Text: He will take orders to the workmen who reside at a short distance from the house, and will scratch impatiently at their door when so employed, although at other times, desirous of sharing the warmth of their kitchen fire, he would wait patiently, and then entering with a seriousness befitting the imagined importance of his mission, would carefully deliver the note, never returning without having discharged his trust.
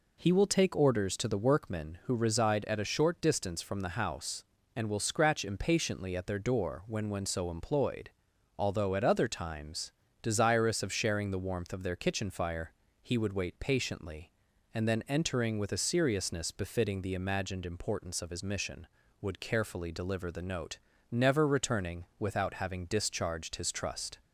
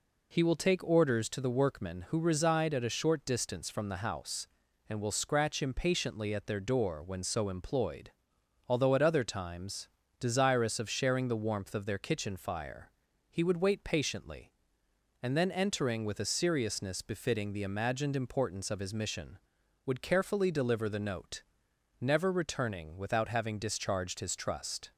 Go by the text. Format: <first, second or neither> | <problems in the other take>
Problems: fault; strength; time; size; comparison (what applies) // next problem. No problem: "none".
second | says "when" twice; at 7.0 s // pauses between "returning" and "without"; slight; at 22.0 s; 0.16 s long